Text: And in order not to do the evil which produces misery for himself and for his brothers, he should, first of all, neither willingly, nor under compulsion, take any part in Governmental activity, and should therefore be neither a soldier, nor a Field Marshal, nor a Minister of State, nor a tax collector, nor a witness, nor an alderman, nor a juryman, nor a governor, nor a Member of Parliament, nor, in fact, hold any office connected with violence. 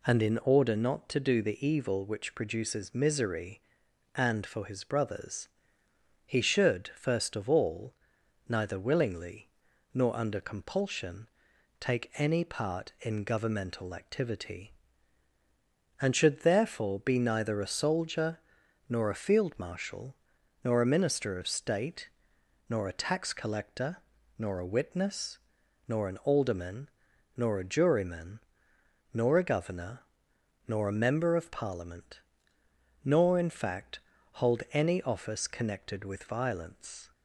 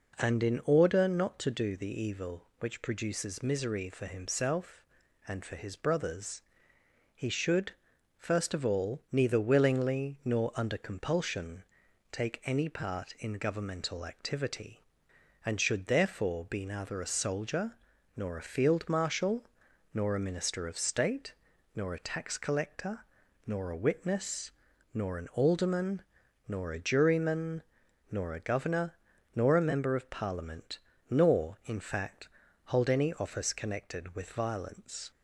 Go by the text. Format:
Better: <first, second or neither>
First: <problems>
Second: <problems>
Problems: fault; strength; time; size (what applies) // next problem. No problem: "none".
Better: second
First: skips "for himself"; at 3.8 s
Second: none